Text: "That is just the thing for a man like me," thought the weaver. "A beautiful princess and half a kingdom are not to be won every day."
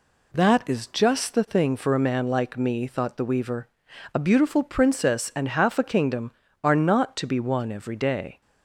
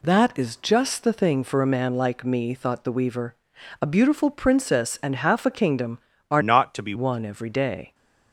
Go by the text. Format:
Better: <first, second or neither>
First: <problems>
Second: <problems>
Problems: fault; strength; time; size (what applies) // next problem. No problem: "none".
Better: first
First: none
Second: changes voice from "not" to "be"; from 6.4 to 6.9 s; 0.5 s long